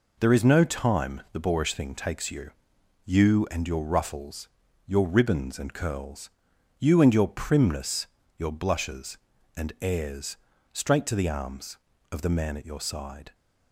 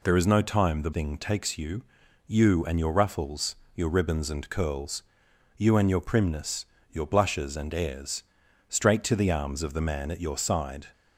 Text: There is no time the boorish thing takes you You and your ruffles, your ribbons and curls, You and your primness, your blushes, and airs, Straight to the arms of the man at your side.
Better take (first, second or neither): first